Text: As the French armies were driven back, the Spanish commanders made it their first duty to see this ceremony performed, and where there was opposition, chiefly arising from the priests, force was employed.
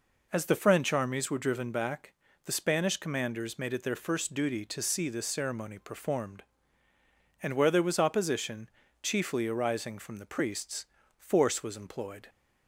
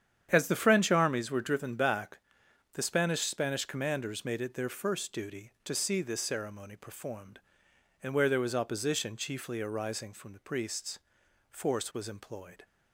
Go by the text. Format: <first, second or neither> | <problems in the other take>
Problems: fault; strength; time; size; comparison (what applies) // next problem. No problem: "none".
first | starts louder than the rest; strong; until 1.3 s; 9 dB // says "Spanish" twice; at 3.2 s